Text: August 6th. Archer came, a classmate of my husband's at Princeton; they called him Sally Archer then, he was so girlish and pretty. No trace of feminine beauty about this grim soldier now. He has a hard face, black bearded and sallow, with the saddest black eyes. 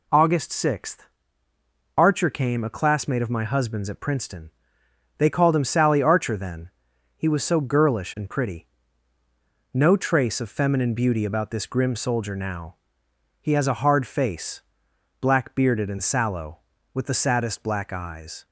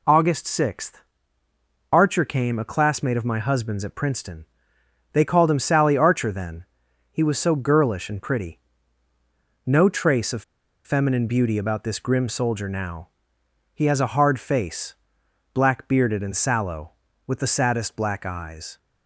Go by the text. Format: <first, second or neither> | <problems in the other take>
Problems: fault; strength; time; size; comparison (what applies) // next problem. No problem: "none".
first | pauses between "of" and "feminine"; at 10.4 s; 0.43 s long